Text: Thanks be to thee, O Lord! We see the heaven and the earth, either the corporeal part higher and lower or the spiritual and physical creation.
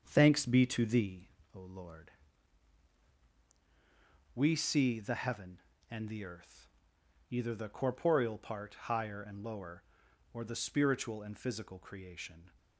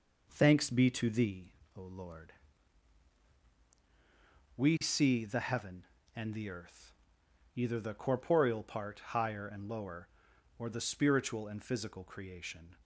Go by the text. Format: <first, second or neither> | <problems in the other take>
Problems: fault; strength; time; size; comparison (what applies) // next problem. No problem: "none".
second | starts louder than the rest; strong; until 1.4 s; 7 dB